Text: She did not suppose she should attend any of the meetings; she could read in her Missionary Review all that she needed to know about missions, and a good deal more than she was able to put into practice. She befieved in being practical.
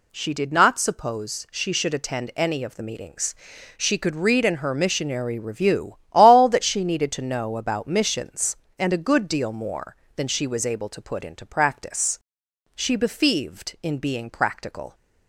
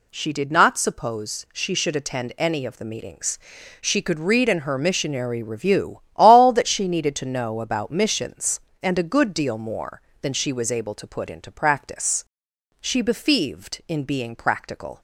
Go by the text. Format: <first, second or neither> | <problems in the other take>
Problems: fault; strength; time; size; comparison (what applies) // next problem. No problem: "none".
neither | pauses between "Review" and "all"; slight; the same in both